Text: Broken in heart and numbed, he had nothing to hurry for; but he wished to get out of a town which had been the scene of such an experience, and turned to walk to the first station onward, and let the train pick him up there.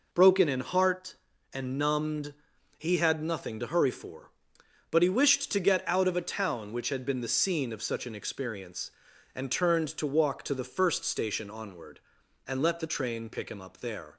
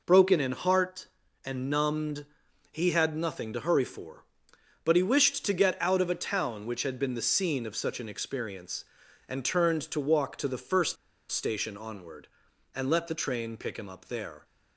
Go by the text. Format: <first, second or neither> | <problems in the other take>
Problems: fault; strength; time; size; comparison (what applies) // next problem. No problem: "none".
first | pauses between "first" and "station"; at 10.9 s; 0.36 s long